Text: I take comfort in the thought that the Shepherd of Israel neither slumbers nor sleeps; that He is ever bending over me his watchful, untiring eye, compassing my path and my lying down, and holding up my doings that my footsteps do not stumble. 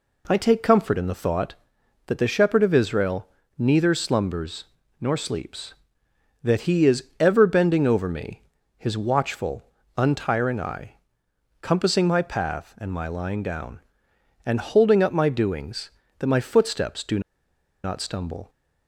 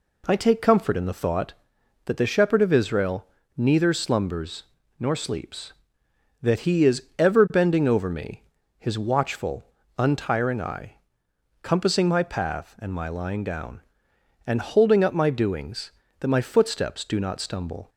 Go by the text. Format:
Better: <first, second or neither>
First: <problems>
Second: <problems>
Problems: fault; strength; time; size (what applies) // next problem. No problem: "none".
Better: second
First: pauses between "Israel" and "neither"; slight; at 3.2 s; 0.30 s long // pauses between "slumbers" and "nor"; slight; at 4.6 s; 0.36 s long // pauses between "is" and "ever"; slight; at 7.0 s; 0.16 s long // pauses between "me" and "his"; slight; at 8.4 s; 0.34 s long // pauses between "do" and "not"; noticeable; at 17.1 s; 0.63 s long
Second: pauses between "Israel" and "neither"; slight; at 3.2 s; 0.30 s long // pauses between "slumbers" and "nor"; slight; at 4.6 s; 0.36 s long // pauses between "is" and "ever"; slight; at 7.0 s; 0.16 s long // pauses between "me" and "his"; slight; at 8.4 s; 0.34 s long